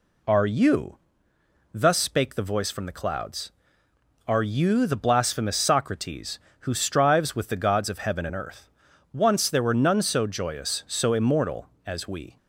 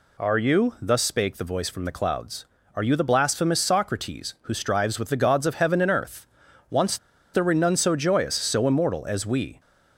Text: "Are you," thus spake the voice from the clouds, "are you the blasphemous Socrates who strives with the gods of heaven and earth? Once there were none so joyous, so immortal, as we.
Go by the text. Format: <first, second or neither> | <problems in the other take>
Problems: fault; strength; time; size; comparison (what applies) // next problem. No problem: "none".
first | pauses between "Once" and "there"; at 6.9 s; 0.36 s long